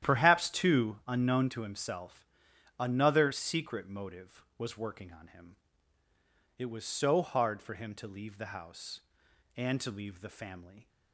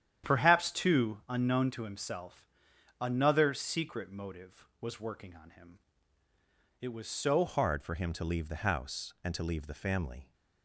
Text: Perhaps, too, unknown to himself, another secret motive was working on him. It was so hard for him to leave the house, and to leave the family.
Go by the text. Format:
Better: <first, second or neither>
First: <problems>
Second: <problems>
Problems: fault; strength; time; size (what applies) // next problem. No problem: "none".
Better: first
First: starts louder than the rest; strong; until 1.1 s; 11 dB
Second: starts louder than the rest; strong; until 1.3 s; 10 dB // changes voice at "hard"; from 7.4 s on; 2.9 s long